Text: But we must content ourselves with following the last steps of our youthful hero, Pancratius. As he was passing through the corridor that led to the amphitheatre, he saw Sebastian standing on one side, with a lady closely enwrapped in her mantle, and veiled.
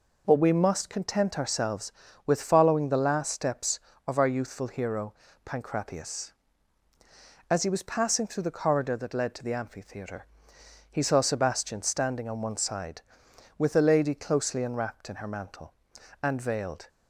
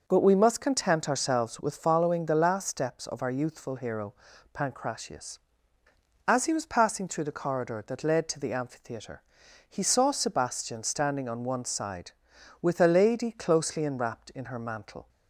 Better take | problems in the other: first | stops before "and veiled"; at 15.0 s

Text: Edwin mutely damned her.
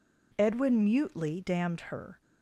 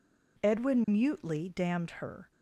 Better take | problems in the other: neither | none

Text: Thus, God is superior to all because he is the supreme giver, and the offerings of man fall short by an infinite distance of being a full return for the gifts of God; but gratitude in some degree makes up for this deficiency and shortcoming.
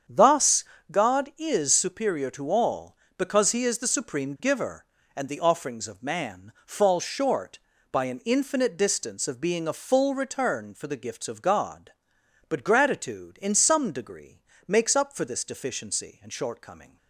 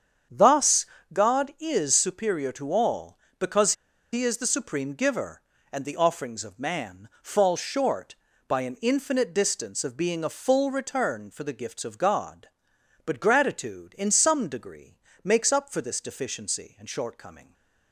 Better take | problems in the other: first | starts louder than the rest; strong; until 1.6 s; 8 dB; strong in the first // pauses between "because" and "he"; at 3.7 s; 0.39 s long // pauses between "degree" and "makes"; slight; at 14.9 s; 0.24 s long; slight in the first

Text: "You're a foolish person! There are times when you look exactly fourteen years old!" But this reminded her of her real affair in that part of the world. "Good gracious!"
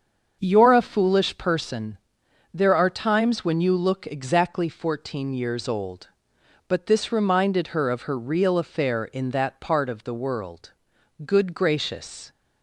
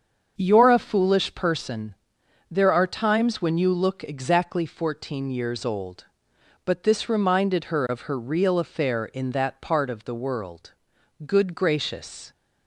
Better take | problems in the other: neither | starts louder than the rest; the same in both

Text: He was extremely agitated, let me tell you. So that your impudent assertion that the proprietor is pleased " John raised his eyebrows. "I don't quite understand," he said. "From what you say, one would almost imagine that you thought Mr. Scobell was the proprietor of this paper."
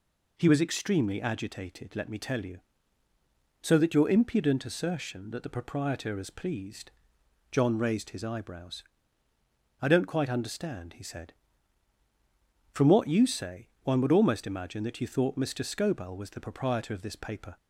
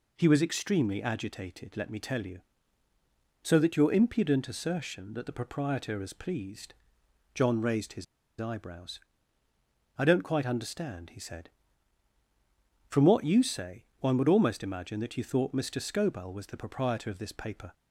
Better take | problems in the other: first | pauses between "his" and "eyebrows"; slight; at 8.0 s; 0.36 s long

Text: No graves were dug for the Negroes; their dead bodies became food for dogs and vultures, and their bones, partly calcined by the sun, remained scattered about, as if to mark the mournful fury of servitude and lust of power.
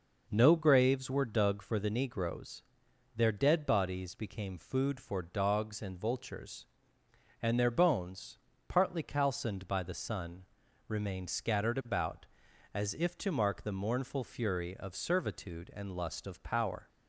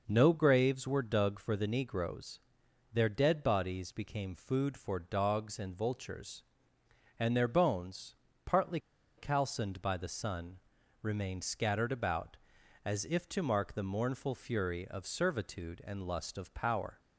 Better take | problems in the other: first | pauses between "partly" and "calcined"; at 8.7 s; 0.39 s long

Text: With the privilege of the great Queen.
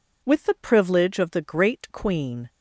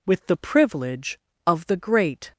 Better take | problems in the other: first | stops before "Queen"; at 2.3 s

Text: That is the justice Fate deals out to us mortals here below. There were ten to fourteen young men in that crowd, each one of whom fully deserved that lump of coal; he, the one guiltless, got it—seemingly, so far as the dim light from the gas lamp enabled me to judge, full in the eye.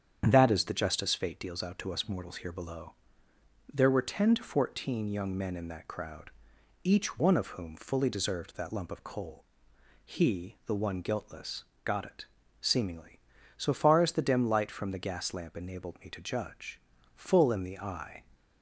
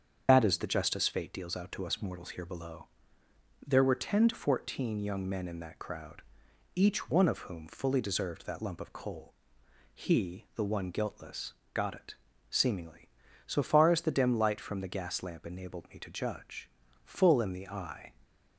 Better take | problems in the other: first | loses the start of "That"; at 0.2 s; 125 ms // starts louder than the rest; strong; until 1.2 s; 7.5 dB; strong in the first

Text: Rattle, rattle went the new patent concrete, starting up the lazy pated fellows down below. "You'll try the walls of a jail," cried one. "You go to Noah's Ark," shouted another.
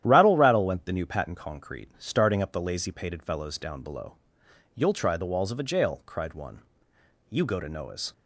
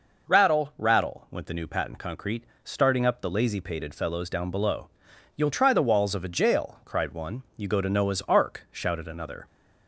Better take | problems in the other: second | starts louder than the rest; strong; until 1.0 s; 11 dB // stops before "Ark shouted another"; at 8.1 s

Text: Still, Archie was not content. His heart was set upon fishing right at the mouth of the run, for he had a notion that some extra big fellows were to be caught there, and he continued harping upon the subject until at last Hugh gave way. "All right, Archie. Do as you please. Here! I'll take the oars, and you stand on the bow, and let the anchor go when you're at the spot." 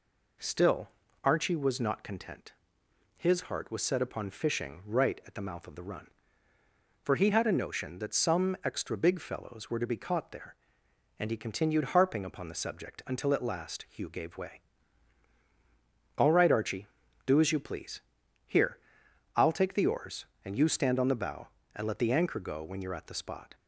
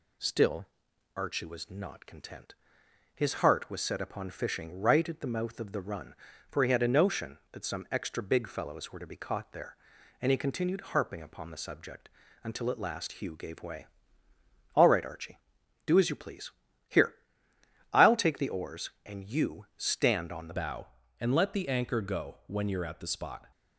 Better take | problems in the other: first | pauses between "subject" and "until"; slight; at 12.0 s; 0.34 s long // changes voice at "bow"; from 20.5 s on; 2.9 s long

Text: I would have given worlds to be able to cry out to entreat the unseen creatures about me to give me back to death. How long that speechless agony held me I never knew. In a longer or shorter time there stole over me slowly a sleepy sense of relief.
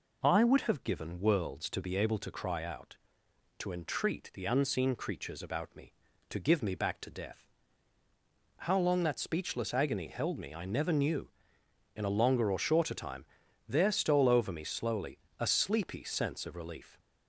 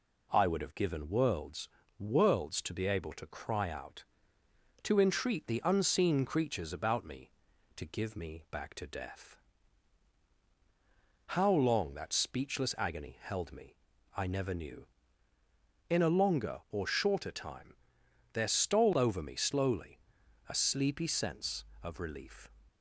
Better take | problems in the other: first | says "worlds" twice; at 1.9 s // pauses between "me" and "I"; at 13.7 s; 0.40 s long // pauses between "time" and "there"; noticeable; at 17.7 s; 0.60 s long; also in the first // pauses between "slowly" and "a"; noticeable; at 19.9 s; 0.50 s long; slight in the first

